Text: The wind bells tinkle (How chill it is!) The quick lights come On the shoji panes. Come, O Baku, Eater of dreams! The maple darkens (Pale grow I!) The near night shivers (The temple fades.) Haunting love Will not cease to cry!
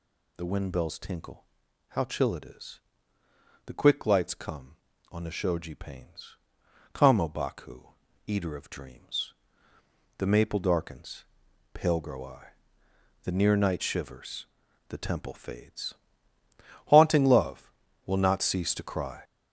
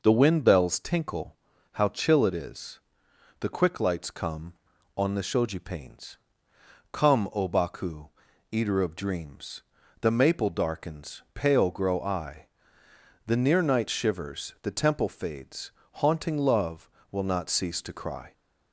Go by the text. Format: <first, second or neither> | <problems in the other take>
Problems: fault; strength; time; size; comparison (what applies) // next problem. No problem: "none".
second | gets louder; throughout; 6.5 dB